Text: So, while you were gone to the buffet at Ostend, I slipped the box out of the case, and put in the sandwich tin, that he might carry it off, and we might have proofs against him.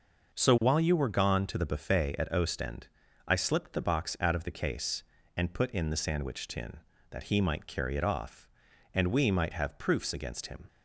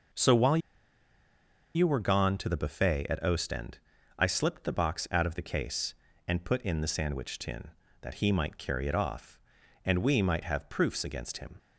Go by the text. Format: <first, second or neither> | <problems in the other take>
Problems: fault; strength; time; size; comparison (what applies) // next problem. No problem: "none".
first | pauses between "while" and "you"; at 0.5 s; 1.1 s long